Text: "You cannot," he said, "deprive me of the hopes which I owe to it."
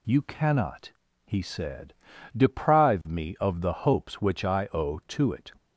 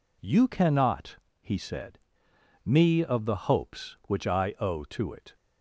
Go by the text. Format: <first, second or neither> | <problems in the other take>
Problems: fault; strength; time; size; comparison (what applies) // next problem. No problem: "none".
first | skips "deprive"; at 2.3 s